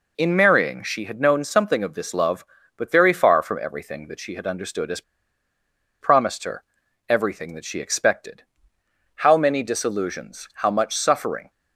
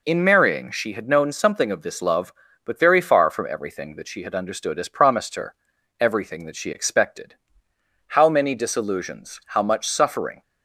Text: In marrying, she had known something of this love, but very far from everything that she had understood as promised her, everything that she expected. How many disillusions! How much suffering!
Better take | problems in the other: second | pauses between "as" and "promised"; at 5.0 s; 0.99 s long

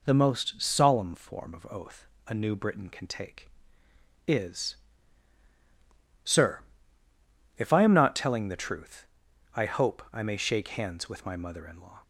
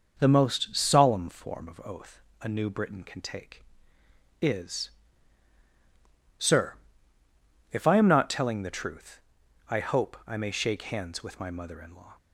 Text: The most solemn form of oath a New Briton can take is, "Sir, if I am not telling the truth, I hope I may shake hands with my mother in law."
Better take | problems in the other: first | starts louder than the rest; noticeable; until 1.7 s; 6 dB // pauses between "oath" and "a"; slight; at 2.2 s; 0.20 s long; slight in the first

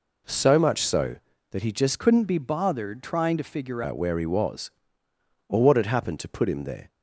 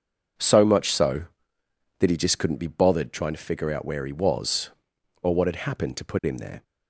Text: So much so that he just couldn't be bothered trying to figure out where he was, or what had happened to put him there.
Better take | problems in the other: second | changes voice from "couldn't" to "figure"; from 1.9 to 3.8 s; 1.9 s long

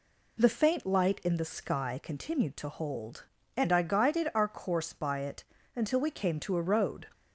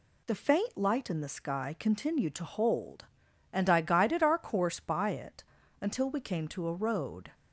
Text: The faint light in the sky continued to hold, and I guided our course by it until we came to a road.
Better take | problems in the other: neither | pauses between "it" and "until"; the same in both

